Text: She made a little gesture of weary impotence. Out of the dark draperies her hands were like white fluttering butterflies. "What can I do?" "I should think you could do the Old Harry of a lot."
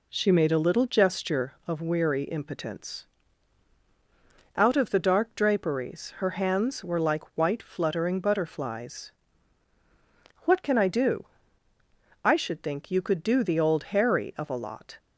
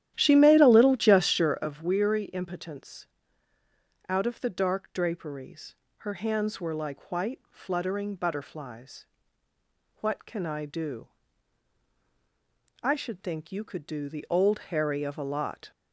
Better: first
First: none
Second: starts louder than the rest; strong; until 1.7 s; 12 dB // pauses between "draperies" and "her"; slight; at 5.7 s; 0.24 s long

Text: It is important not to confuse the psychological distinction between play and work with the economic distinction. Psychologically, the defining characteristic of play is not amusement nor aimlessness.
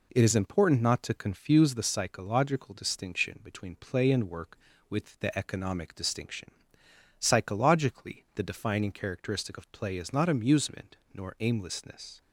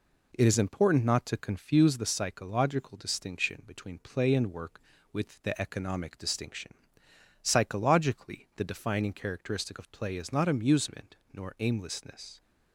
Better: neither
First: pauses between "amusement" and "nor"; slight; at 10.9 s; 0.16 s long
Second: pauses between "amusement" and "nor"; slight; at 11.1 s; 0.16 s long

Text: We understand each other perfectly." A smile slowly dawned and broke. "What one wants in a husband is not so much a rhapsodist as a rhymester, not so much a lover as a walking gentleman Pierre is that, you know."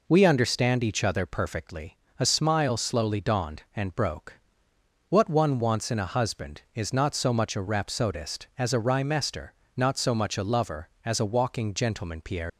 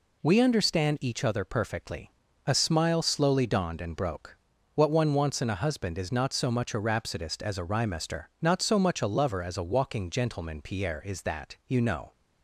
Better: second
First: stops before "is that you know"; at 12.4 s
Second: none

